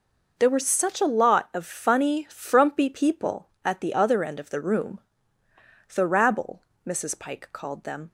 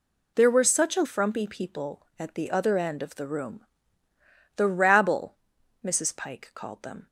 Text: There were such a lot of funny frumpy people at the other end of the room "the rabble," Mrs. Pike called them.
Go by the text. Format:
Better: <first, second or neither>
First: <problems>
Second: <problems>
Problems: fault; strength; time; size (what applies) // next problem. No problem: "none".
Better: first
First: pauses between "room" and "the"; noticeable; at 4.9 s; 0.96 s long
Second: skips "lot of funny"; at 1.0 s // pauses between "room" and "the"; noticeable; at 3.6 s; 0.92 s long